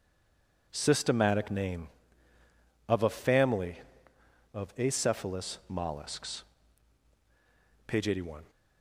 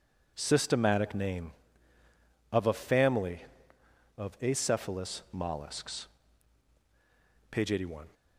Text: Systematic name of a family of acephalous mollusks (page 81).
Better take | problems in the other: second | stays silent before the first word; slight; until 0.7 s; 0.7 s long

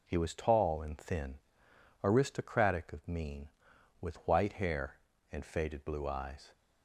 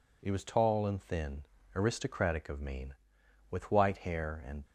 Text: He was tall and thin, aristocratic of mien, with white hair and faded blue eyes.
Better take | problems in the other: first | stops before "faded blue eyes"; at 4.6 s

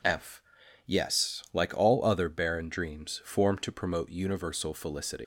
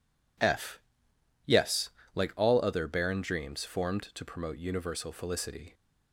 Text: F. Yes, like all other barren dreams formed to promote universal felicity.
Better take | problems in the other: second | leaves "felicity" unfinished; at 5.2 s; 110 ms

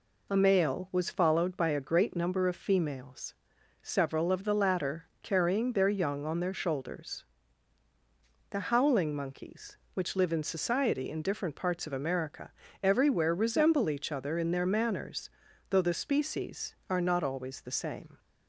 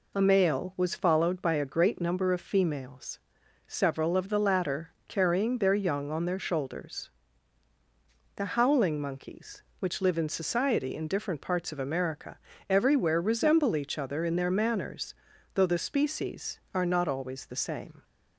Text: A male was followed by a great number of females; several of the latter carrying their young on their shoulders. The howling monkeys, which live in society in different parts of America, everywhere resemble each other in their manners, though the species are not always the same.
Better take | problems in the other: neither | pauses between "latter" and "carrying"; slight; the same in both

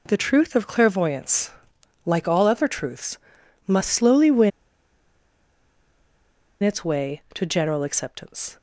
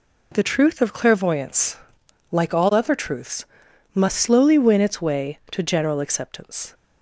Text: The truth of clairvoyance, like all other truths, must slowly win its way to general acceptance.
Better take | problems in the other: second | pauses between "win" and "its"; strong; at 4.5 s; 2.1 s long

